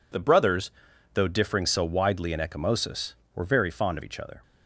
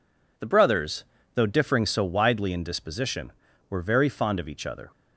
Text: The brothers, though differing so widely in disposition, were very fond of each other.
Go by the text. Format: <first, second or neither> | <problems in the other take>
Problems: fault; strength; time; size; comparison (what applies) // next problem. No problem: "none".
second | says "ecchymosis" for "disposition"; at 2.3 s